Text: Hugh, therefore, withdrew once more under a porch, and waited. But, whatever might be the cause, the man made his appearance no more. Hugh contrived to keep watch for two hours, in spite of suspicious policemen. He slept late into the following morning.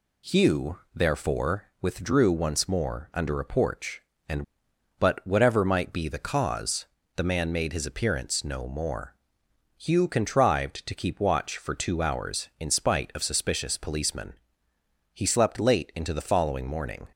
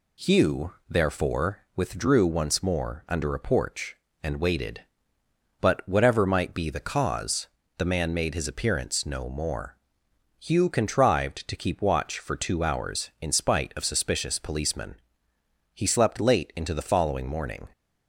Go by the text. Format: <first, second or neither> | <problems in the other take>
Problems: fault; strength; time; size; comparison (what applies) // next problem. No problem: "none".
second | skips "waited"; at 4.7 s